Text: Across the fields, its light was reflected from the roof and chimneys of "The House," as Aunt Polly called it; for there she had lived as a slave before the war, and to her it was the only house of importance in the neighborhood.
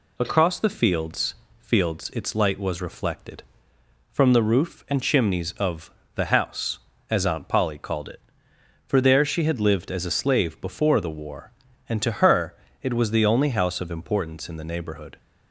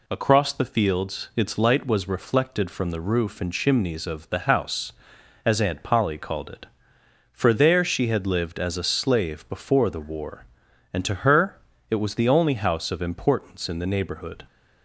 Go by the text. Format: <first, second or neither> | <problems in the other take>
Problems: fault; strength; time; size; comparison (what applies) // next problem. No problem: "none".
second | says "fields" twice; at 1.5 s // pauses between "of" and "The"; slight; at 5.9 s; 0.24 s long // pauses between "her" and "it"; slight; at 12.5 s; 0.26 s long; slight in the second